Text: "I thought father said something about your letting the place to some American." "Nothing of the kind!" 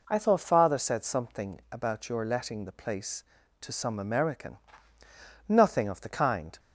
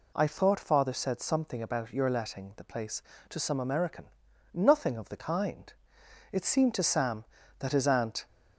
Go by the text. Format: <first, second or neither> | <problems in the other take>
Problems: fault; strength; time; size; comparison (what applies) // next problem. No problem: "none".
first | goes on to say "It seemed to Sam that his aunt"; strong; from 6.3 s on; 1.9 s long